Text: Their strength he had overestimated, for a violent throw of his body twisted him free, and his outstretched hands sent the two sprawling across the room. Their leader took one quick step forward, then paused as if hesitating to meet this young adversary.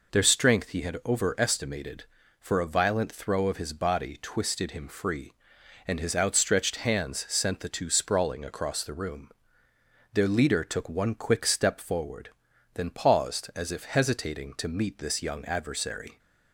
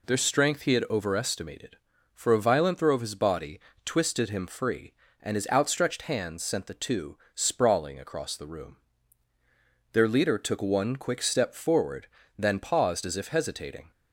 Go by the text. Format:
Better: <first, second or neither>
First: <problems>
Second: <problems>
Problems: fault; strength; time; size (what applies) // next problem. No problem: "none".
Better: first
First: none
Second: pauses between "body" and "twisted"; slight; at 3.5 s; 0.26 s long // pauses between "two" and "sprawling"; slight; at 7.1 s; 0.18 s long // stops before "to meet this young adversary"; at 13.9 s